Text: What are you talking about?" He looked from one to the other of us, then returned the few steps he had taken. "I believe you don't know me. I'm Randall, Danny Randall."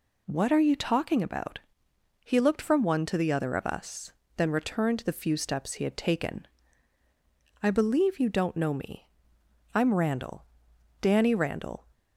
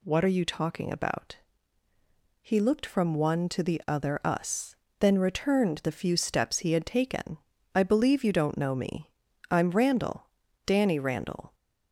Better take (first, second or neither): first